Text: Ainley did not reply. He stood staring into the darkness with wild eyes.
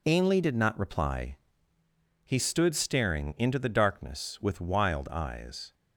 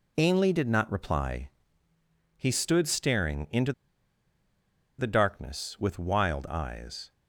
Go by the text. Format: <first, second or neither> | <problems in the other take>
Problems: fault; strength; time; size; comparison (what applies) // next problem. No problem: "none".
first | pauses between "into" and "the"; strong; at 3.7 s; 1.2 s long